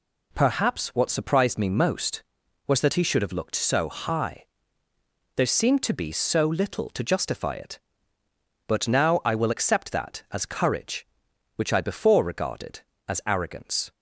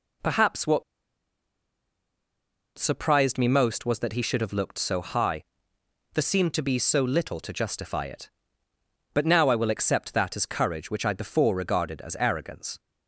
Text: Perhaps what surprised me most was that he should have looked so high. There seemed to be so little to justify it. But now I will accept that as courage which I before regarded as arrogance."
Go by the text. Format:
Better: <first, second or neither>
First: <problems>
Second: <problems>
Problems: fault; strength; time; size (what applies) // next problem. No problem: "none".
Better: first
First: none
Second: pauses between "what" and "surprised"; strong; at 0.8 s; 1.9 s long